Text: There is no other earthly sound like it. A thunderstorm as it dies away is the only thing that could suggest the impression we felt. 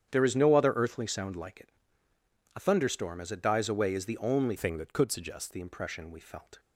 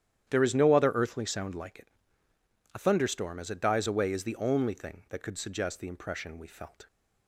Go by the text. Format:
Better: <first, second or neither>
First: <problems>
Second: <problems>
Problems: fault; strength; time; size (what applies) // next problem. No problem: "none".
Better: second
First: starts louder than the rest; strong; until 1.1 s; 9 dB // changes voice from "thing" to "suggest"; from 4.5 to 5.5 s; 1.0 s long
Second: starts louder than the rest; strong; until 1.3 s; 10.5 dB